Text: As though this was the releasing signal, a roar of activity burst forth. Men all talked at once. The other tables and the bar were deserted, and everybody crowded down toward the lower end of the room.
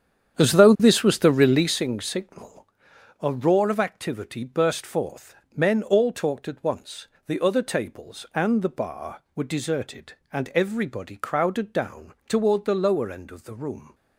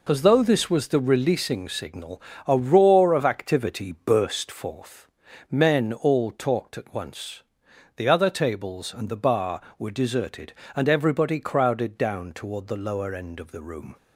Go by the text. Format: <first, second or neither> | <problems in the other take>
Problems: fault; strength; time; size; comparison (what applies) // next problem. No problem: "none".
second | starts louder than the rest; strong; until 1.8 s; 9 dB // pauses between "down" and "toward"; slight; at 12.1 s; 0.16 s long